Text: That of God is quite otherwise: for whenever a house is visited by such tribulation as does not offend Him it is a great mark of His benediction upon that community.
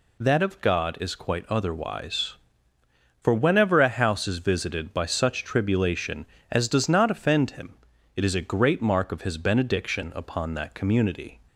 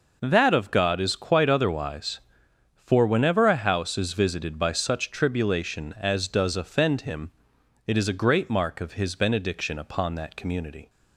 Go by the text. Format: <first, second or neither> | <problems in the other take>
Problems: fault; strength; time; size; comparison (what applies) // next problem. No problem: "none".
first | skips "not"; at 6.5 s // pauses between "Him" and "it"; noticeable; at 7.3 s; 0.56 s long; also in the first